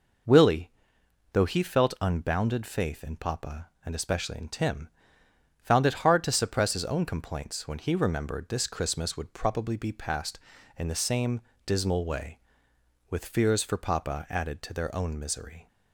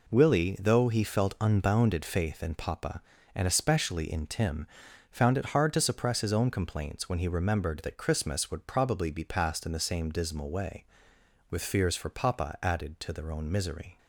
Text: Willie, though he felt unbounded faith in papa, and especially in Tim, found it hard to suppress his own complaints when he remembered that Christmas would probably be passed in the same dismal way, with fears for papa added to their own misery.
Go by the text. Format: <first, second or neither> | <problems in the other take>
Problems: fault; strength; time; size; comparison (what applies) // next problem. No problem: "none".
second | says "this" for "that"; at 8.4 s // pauses between "same" and "dismal"; slight; at 11.4 s; 0.24 s long